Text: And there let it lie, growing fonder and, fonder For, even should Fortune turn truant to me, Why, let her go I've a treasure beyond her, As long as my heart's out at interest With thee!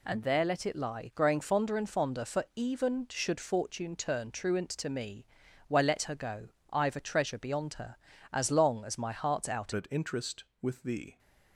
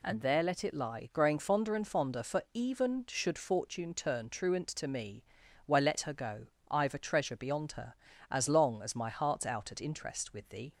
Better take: second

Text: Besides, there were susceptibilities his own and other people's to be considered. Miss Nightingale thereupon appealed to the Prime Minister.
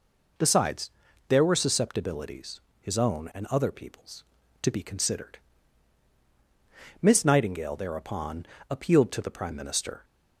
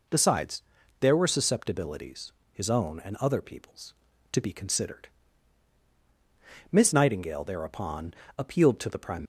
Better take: first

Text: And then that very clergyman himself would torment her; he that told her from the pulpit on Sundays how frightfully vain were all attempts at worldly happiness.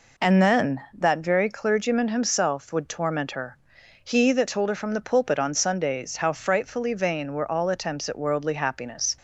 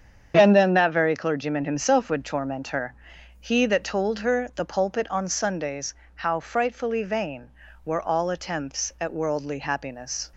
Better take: first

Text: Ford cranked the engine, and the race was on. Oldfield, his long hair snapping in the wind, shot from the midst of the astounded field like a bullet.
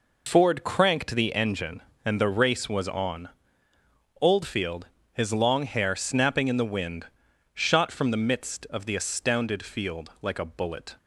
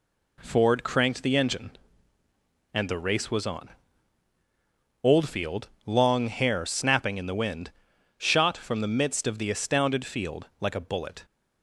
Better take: first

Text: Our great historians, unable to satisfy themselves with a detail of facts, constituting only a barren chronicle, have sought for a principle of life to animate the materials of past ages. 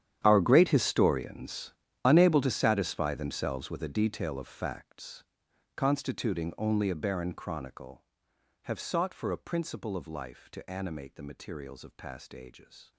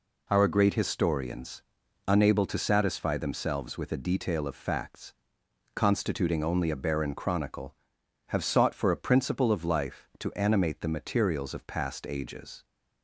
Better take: second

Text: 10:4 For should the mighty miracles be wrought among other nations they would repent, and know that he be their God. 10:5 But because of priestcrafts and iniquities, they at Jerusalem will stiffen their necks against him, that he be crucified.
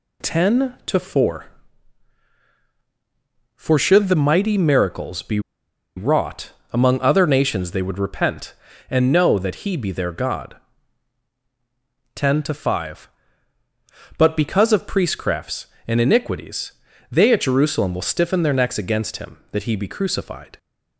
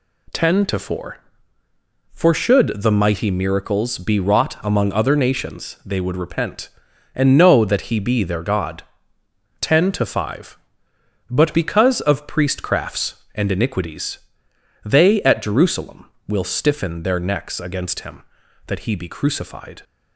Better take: second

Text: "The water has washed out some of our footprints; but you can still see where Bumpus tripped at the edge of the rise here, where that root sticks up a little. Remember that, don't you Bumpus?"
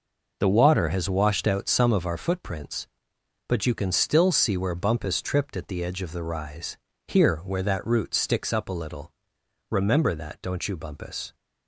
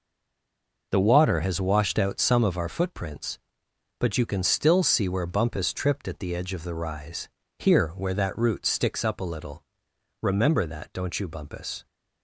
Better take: first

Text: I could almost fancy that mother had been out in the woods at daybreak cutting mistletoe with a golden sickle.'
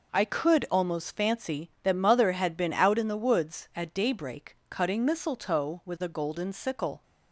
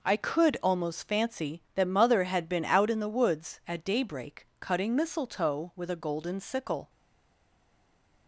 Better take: first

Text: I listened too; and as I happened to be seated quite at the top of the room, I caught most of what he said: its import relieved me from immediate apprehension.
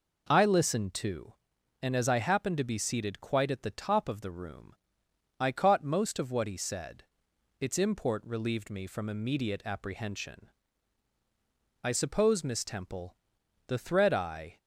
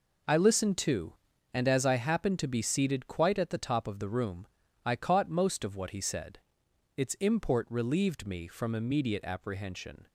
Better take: second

